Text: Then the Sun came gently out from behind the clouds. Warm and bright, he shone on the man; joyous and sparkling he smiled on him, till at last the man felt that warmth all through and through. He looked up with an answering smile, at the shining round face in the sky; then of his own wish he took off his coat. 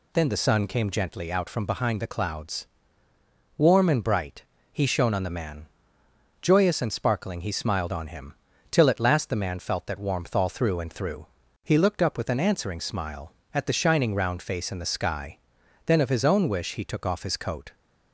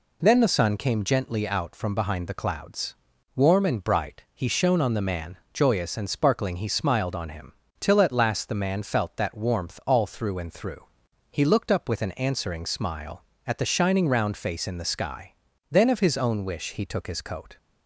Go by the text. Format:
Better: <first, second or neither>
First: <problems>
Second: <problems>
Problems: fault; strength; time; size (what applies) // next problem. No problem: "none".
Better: first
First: none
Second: skips "off"; at 17.0 s